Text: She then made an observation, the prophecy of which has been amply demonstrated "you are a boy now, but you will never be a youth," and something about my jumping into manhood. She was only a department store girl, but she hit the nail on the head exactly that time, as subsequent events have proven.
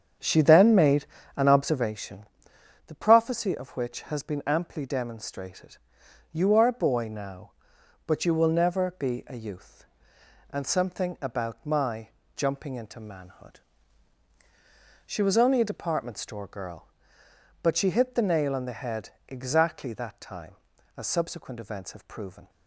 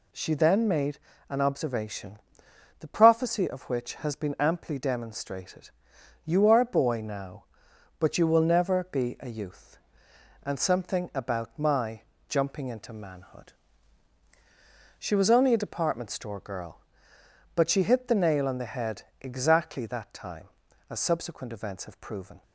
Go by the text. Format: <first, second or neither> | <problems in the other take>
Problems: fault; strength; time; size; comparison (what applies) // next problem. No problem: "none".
second | starts louder than the rest; strong; until 2.0 s; 8 dB // pauses between "made" and "an"; slight; at 1.0 s; 0.32 s long; slight in the second // pauses between "demonstrated" and "you"; noticeable; at 5.7 s; 0.56 s long; noticeable in the second // pauses between "my" and "jumping"; slight; at 12.0 s; 0.26 s long; slight in the second // pauses between "head" and "exactly"; slight; at 19.1 s; 0.18 s long; slight in the second